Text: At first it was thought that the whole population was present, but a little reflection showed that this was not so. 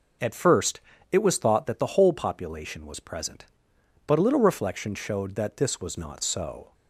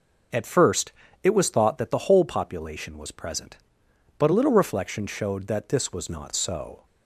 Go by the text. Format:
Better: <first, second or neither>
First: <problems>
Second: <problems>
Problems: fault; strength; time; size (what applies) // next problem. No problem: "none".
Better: neither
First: pauses between "first" and "it"; slight; at 0.7 s; 0.32 s long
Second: pauses between "first" and "it"; slight; at 0.9 s; 0.32 s long